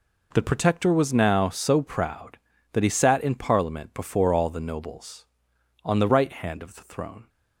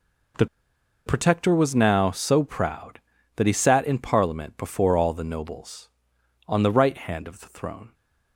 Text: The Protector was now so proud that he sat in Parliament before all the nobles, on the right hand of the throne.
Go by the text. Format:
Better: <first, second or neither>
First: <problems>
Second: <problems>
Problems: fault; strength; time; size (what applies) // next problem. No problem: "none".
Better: first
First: none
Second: pauses between "The" and "Protector"; noticeable; at 0.4 s; 0.60 s long